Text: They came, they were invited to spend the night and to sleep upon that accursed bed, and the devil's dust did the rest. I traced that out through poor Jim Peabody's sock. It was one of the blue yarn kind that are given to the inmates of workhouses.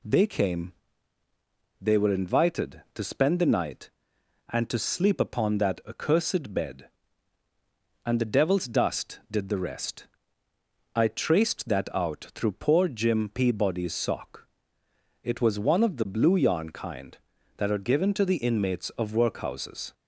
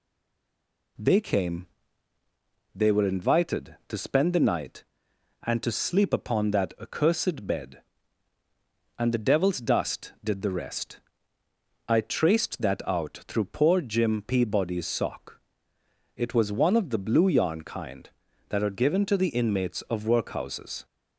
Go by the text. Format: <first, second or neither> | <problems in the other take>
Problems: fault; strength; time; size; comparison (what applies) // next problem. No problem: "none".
first | stays silent before the first word; slight; until 0.9 s; 0.9 s long